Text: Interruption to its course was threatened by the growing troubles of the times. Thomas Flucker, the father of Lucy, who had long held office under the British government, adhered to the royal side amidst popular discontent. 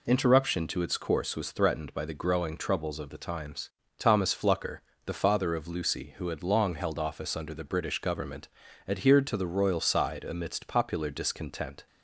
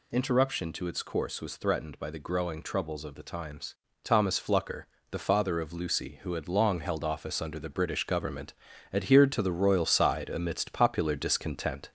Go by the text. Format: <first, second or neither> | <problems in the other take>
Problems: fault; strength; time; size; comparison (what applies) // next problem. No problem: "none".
first | gets louder; slight; throughout; 3 dB